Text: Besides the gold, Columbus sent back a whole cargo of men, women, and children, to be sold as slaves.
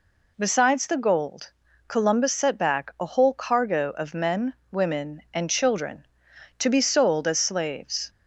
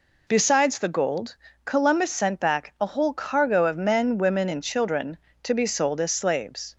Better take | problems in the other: second | says "set" for "sent"; at 2.3 s

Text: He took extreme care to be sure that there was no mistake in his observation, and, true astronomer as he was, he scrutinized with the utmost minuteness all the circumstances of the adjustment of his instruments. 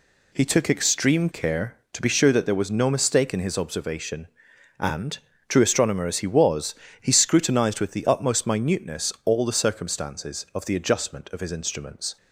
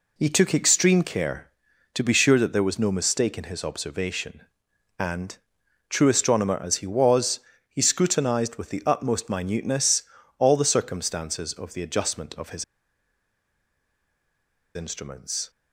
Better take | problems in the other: first | pauses between "minuteness" and "all"; at 10.0 s; 0.38 s long // pauses between "his" and "instruments"; strong; at 12.6 s; 2.1 s long

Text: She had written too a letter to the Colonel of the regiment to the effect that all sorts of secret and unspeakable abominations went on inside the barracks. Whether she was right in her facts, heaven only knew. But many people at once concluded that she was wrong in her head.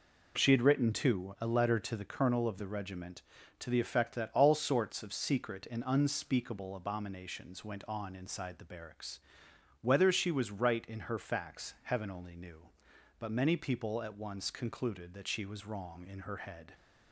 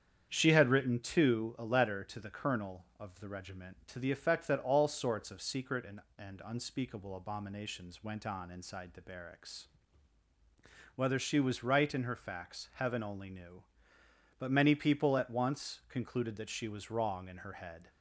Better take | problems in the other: first | starts louder than the rest; strong; until 1.3 s; 8.5 dB // says "and" twice; at 6.1 s

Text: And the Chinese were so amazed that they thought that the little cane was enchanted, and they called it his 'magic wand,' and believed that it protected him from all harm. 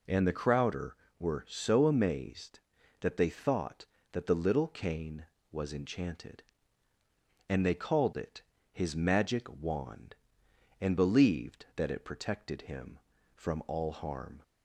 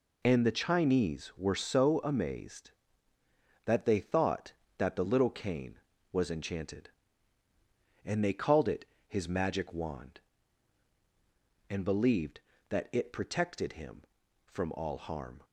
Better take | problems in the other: second | says "Crowder" for "Chinese"; at 0.3 s // pauses between "it" and "his"; slight; at 8.4 s; 0.28 s long; slight in the second

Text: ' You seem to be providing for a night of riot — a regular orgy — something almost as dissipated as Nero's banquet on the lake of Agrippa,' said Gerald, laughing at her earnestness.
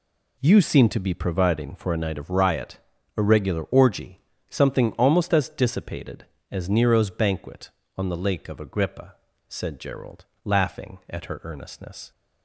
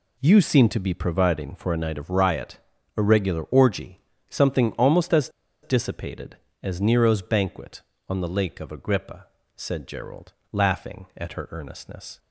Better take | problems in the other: first | pauses between "as" and "dissipated"; slight; at 5.2 s; 0.34 s long

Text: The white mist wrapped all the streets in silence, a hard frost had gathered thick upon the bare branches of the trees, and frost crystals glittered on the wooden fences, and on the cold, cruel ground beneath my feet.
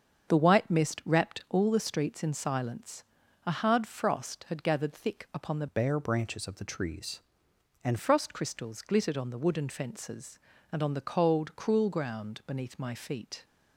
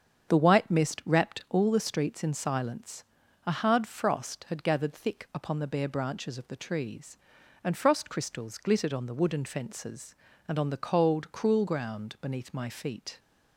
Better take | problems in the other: second | starts louder than the rest; until 1.3 s; 7 dB; strong in the second // changes voice from "bare" to "and"; from 5.6 to 7.9 s; 2.3 s long

